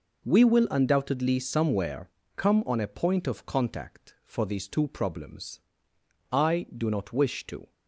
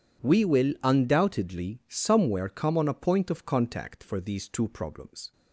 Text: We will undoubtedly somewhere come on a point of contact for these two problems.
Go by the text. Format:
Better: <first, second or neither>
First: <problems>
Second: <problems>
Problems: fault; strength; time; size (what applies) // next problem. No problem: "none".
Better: second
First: pauses between "somewhere" and "come"; slight; at 2.0 s; 0.28 s long // goes on to say "I do not wish to"; from 6.3 s on; 1.4 s long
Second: none